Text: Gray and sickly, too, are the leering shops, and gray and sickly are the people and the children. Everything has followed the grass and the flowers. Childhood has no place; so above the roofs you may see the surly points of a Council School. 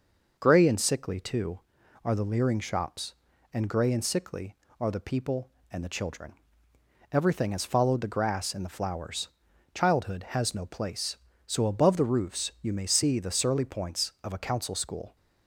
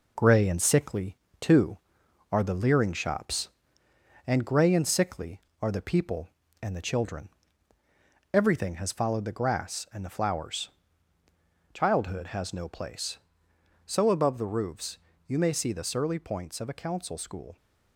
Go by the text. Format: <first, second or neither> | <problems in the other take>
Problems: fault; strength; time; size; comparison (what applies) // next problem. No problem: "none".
first | gets quieter; noticeable; throughout; 5 dB // pauses between "roofs" and "you"; slight; at 14.9 s; 0.28 s long